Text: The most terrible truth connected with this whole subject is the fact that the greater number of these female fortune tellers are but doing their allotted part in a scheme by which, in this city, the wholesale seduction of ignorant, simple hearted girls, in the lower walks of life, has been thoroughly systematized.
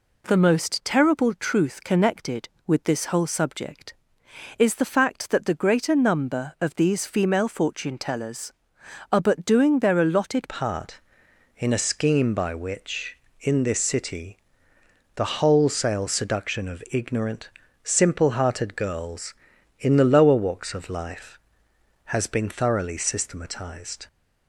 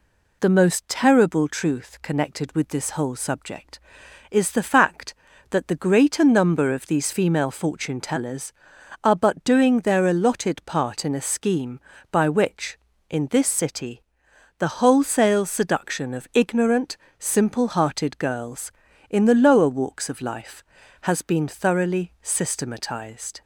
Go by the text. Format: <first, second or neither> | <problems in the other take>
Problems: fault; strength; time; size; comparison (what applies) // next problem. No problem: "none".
second | changes voice at "part"; from 10.4 s on; 13.6 s long